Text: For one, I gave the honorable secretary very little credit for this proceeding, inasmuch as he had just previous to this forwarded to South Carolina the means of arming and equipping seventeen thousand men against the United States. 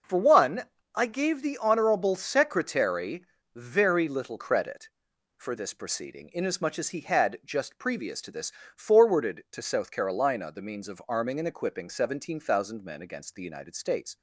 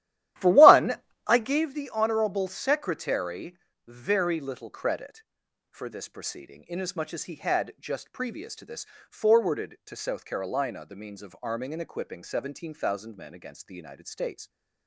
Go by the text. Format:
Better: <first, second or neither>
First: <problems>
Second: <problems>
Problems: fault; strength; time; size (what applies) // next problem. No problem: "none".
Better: first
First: pauses between "secretary" and "very"; slight; at 3.2 s; 0.32 s long // pauses between "this" and "forwarded"; slight; at 8.5 s; 0.24 s long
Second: starts louder than the rest; strong; until 1.7 s; 13 dB // pauses between "secretary" and "very"; slight; at 3.5 s; 0.32 s long // pauses between "this" and "forwarded"; slight; at 8.8 s; 0.24 s long